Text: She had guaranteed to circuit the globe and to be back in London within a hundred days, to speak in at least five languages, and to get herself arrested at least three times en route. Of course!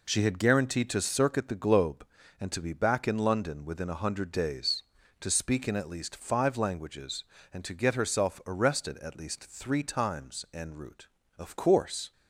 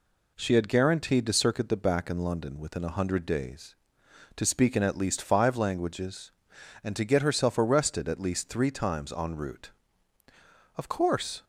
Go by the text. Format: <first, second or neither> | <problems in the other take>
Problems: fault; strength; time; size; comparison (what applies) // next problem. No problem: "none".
first | skips "globe and to be"; at 1.7 s